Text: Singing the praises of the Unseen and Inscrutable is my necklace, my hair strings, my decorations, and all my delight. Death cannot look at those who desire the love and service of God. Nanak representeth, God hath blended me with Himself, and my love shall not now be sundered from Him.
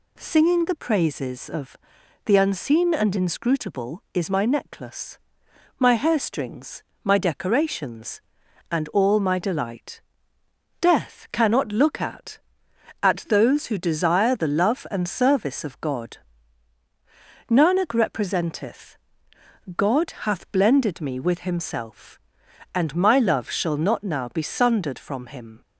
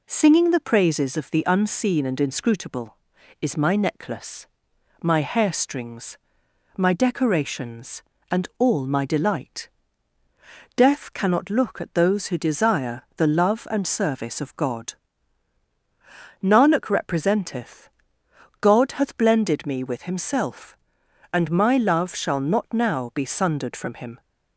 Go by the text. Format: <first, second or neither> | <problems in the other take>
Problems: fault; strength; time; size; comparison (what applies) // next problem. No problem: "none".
second | pauses between "of" and "the"; noticeable; at 1.7 s; 0.48 s long // says "at" twice; at 13.0 s